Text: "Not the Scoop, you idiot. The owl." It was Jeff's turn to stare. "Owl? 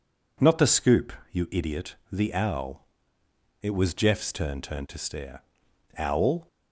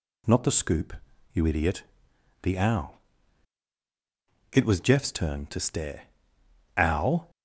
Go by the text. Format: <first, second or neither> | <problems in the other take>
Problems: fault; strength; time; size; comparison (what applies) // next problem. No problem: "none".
second | says "turn" twice; at 4.6 s